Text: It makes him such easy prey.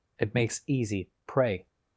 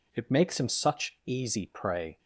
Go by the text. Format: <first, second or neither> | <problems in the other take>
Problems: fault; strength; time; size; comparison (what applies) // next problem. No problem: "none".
second | skips "him such"; at 0.6 s // pauses between "easy" and "prey"; slight; at 1.1 s; 0.16 s long